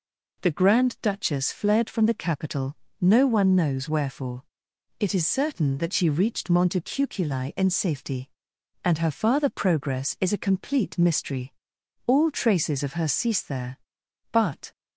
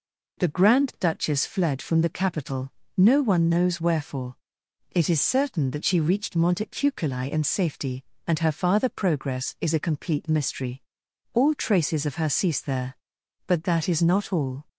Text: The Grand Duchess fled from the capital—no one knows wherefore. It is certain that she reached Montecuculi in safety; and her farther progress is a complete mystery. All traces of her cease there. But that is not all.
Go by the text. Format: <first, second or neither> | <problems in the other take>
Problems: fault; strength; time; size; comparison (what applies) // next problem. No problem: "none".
second | stops before "that is not all"; at 14.7 s